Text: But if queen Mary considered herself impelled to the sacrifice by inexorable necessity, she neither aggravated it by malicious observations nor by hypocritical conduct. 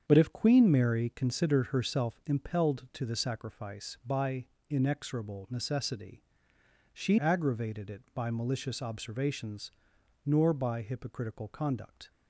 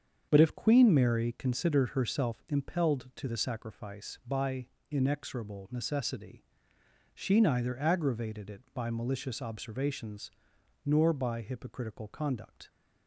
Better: second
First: starts louder than the rest; strong; until 1.0 s; 7.5 dB // pauses between "by" and "inexorable"; slight; at 4.4 s; 0.22 s long // skips "neither"; at 7.1 s // pauses between "observations" and "nor"; noticeable; at 9.7 s; 0.54 s long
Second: starts louder than the rest; strong; until 1.3 s; 7 dB // pauses between "by" and "inexorable"; slight; at 4.6 s; 0.22 s long // pauses between "observations" and "nor"; noticeable; at 10.3 s; 0.54 s long

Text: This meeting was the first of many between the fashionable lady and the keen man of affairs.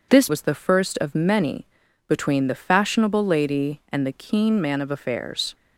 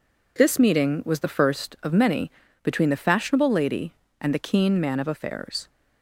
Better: second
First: skips "meeting"; at 0.2 s // pauses between "many" and "between"; at 1.6 s; 0.42 s long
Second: pauses between "many" and "between"; slight; at 2.2 s; 0.32 s long

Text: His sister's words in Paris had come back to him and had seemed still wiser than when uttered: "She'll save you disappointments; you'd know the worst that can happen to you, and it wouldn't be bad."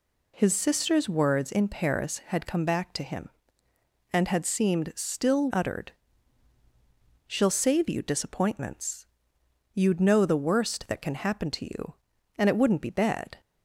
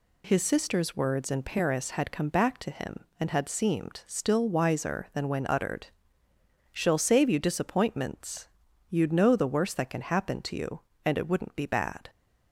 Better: second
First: skips "wiser than when"; at 5.5 s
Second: none

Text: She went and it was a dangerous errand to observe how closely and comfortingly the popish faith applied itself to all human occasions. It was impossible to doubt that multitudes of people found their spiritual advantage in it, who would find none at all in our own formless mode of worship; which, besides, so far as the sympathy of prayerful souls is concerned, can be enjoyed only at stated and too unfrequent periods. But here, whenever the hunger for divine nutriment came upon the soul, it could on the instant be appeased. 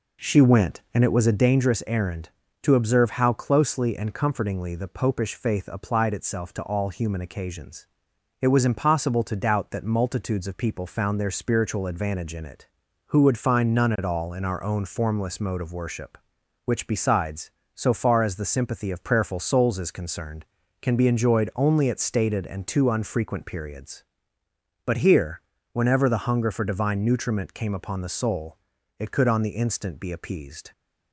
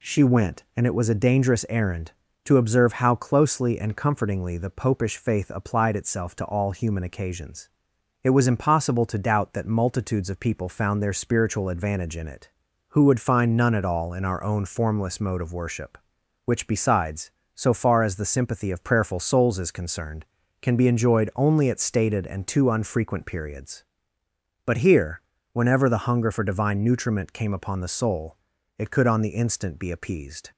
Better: second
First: starts louder than the rest; noticeable; until 1.6 s; 4 dB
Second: none

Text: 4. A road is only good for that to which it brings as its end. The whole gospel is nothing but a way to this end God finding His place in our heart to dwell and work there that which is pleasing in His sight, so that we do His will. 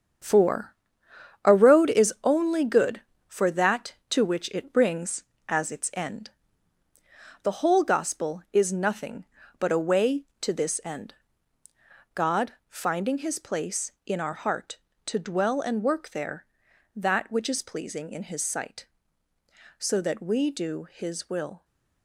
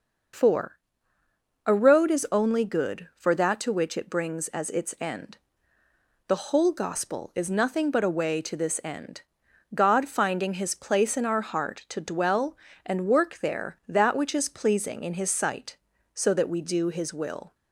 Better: second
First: gets quieter; strong; throughout; 8.5 dB // pauses between "end" and "God"; at 11.1 s; 1.0 s long // pauses between "God" and "finding"; slight; at 12.5 s; 0.16 s long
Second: pauses between "end" and "God"; noticeable; at 9.2 s; 0.52 s long

